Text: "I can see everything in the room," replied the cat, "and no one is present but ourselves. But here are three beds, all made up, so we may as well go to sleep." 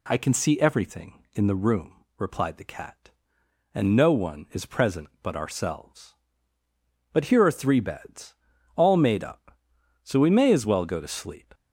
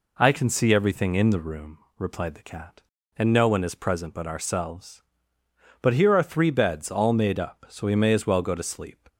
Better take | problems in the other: neither | none

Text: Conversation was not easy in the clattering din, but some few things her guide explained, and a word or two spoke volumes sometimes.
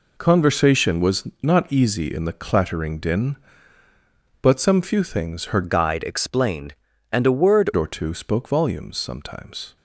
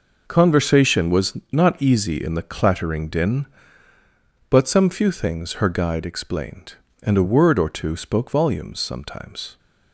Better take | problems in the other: second | pauses between "was" and "not"; slight; at 1.2 s; 0.16 s long; slight in the second // changes voice from "guide" to "word"; from 5.6 to 7.7 s; 2.1 s long

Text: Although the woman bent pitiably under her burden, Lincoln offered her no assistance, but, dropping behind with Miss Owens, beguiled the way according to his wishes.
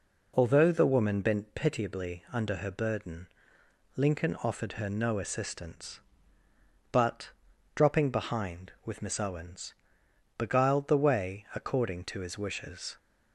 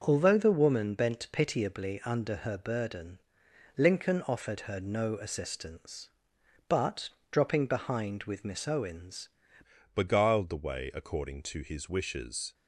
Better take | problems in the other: first | starts louder than the rest; until 1.0 s; 6 dB // changes voice at "beguiled"; from 9.9 s on; 2.6 s long

